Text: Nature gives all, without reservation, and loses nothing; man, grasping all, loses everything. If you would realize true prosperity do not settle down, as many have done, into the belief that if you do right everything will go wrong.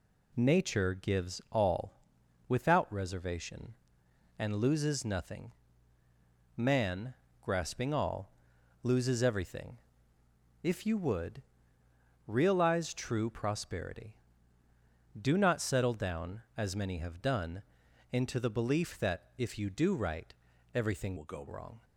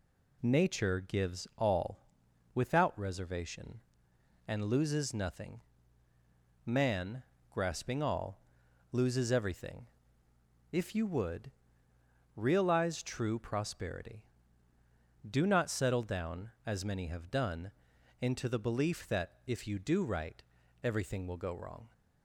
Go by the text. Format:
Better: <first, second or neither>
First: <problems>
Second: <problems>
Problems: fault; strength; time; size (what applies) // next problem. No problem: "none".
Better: second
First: pauses between "would" and "realize"; noticeable; at 11.4 s; 0.82 s long // pauses between "right" and "everything"; at 20.3 s; 0.40 s long // changes voice from "will" to "go"; from 21.1 to 21.4 s; 0.3 s long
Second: pauses between "would" and "realize"; noticeable; at 11.5 s; 0.82 s long // pauses between "right" and "everything"; at 20.4 s; 0.40 s long